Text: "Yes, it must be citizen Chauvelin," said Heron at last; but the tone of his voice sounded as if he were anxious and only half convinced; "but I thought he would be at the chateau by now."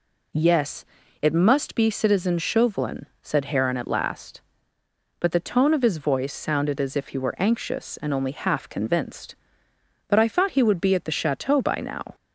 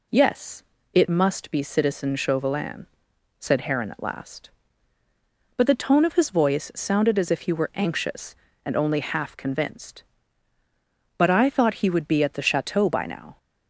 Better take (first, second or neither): neither